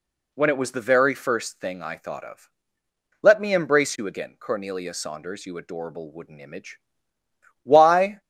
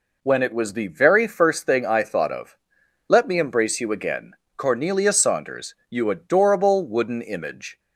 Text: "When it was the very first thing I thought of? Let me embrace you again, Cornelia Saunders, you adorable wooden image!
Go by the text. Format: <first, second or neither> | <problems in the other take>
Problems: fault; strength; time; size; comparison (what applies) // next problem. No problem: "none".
second | goes on to say "Why"; from 7.6 s on; 0.58 s long